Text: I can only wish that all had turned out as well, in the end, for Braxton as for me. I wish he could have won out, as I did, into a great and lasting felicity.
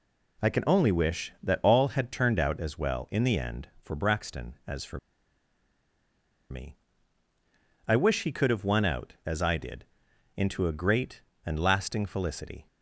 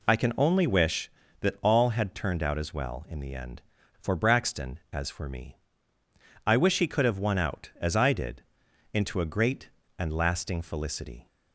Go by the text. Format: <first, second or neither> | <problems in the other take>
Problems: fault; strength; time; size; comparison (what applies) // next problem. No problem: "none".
second | pauses between "for" and "me"; strong; at 4.9 s; 1.5 s long